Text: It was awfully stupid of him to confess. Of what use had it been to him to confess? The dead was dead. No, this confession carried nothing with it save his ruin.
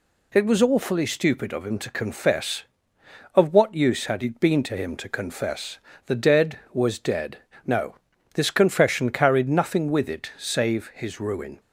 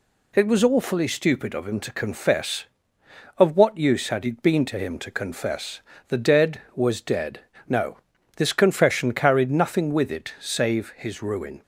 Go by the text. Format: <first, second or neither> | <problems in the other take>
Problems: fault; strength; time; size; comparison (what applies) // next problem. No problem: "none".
neither | none